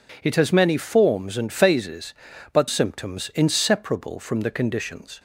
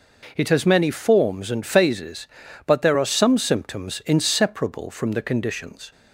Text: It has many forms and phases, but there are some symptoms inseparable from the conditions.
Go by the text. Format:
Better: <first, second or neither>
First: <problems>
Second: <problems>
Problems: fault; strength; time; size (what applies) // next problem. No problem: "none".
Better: second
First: skips "there are some"; at 2.6 s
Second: none